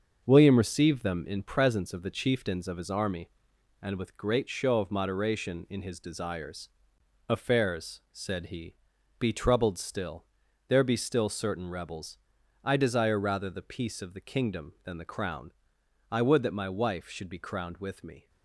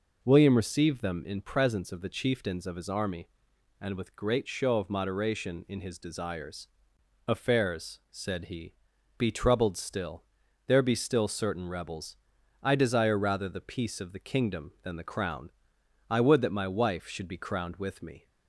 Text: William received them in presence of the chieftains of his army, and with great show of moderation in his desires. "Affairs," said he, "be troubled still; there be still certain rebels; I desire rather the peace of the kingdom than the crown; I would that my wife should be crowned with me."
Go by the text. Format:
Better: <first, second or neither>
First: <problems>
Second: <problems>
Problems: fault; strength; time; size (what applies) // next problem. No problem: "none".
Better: second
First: gets quieter; noticeable; throughout; 6 dB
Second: none